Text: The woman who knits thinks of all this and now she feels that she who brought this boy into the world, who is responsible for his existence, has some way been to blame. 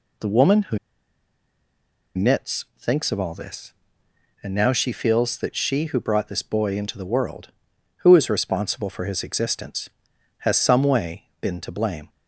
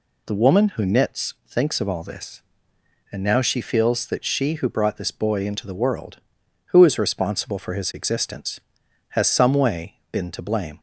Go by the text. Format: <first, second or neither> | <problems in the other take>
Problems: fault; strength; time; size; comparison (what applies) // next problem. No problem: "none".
second | pauses between "who" and "knits"; strong; at 0.7 s; 1.3 s long